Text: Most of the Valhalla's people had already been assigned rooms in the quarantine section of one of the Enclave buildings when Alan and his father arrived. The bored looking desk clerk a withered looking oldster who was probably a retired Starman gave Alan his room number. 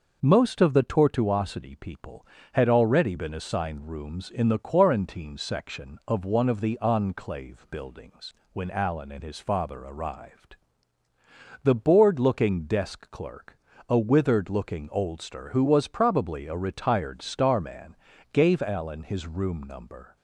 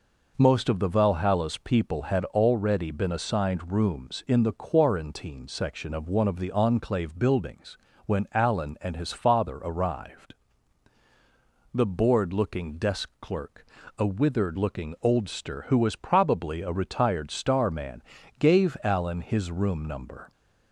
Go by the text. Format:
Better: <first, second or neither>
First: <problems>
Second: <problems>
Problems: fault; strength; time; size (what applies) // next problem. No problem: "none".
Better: second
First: says "Tortuosity" for "Valhalla's"; at 0.8 s // pauses between "buildings" and "when"; slight; at 8.3 s; 0.20 s long // pauses between "clerk" and "a"; slight; at 13.5 s; 0.32 s long // pauses between "Starman" and "gave"; slight; at 17.9 s; 0.36 s long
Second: pauses between "buildings" and "when"; slight; at 7.7 s; 0.28 s long // pauses between "clerk" and "a"; slight; at 13.6 s; 0.32 s long // pauses between "Starman" and "gave"; at 18.0 s; 0.38 s long